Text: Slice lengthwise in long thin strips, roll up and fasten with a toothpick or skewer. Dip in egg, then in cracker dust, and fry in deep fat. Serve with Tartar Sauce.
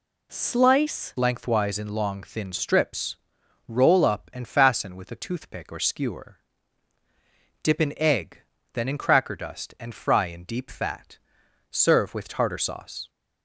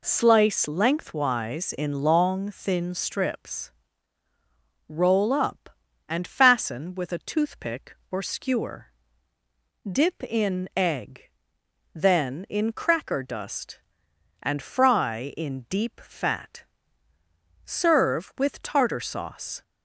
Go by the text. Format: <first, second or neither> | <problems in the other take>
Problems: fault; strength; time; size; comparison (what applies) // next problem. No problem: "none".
second | changes voice at "lengthwise"; from 1.1 s on; 11.9 s long